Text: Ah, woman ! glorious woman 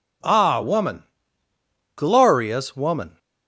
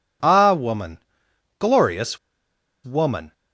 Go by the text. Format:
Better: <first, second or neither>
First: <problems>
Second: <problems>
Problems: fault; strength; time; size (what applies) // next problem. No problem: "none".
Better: first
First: none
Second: pauses between "glorious" and "woman"; noticeable; at 2.1 s; 0.66 s long